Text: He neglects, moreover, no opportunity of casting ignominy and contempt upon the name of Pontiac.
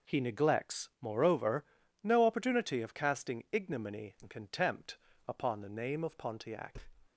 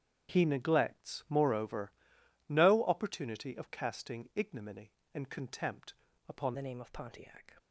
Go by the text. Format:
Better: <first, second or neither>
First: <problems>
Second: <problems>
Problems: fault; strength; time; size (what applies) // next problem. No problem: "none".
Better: first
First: pauses between "contempt" and "upon"; slight; at 4.9 s; 0.28 s long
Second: starts louder than the rest; strong; until 1.3 s; 9 dB // pauses between "contempt" and "upon"; slight; at 5.9 s; 0.34 s long // changes voice at "the"; from 6.5 s on; 1.0 s long